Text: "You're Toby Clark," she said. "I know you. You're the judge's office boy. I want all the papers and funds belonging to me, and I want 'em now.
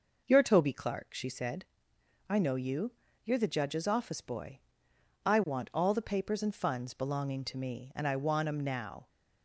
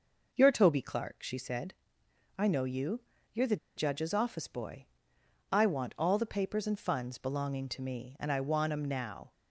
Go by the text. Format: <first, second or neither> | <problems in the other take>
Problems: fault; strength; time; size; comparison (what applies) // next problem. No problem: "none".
first | pauses between "the" and "judge's"; slight; at 3.5 s; 0.20 s long